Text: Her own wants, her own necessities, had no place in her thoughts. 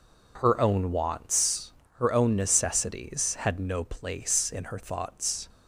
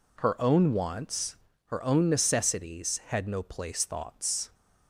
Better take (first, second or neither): first